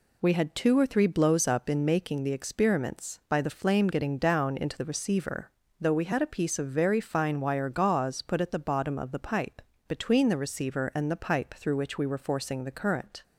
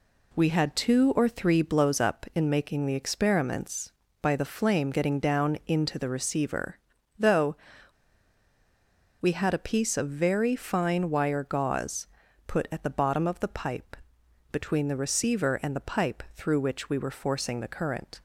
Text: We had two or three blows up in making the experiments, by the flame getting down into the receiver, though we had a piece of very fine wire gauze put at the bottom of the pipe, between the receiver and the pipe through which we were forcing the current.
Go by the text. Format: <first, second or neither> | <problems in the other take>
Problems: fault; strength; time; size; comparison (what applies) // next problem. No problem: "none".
first | pauses between "though" and "we"; strong; at 7.5 s; 1.6 s long // pauses between "gauze" and "put"; at 12.0 s; 0.40 s long